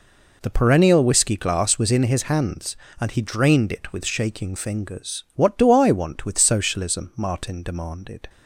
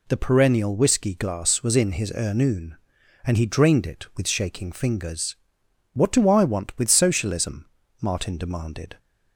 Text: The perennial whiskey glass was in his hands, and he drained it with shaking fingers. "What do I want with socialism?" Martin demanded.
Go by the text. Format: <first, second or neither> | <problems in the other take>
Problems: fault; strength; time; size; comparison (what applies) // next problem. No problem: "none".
first | says "ernoon" for "hands"; at 2.1 s